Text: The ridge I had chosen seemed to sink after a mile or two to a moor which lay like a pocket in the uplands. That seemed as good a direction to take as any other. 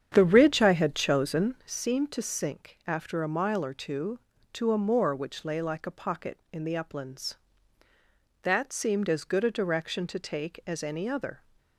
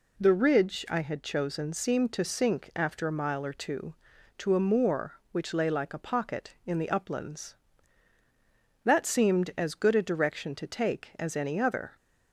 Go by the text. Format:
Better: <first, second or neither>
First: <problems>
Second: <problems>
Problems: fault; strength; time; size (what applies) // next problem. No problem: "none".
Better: second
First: starts louder than the rest; strong; until 1.8 s; 8.5 dB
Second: none